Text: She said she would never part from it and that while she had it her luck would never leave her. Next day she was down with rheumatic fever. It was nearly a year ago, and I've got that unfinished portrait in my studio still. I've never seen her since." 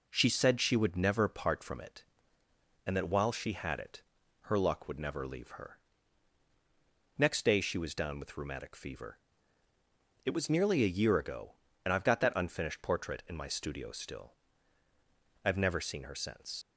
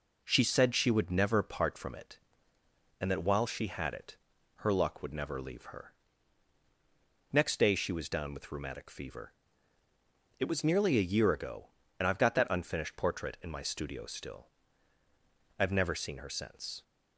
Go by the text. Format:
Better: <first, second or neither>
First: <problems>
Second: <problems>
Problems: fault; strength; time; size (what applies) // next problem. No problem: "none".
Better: second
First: pauses between "it" and "her"; at 4.0 s; 0.40 s long // leaves "since" unfinished; at 16.6 s; 65 ms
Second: pauses between "it" and "her"; at 4.1 s; 0.40 s long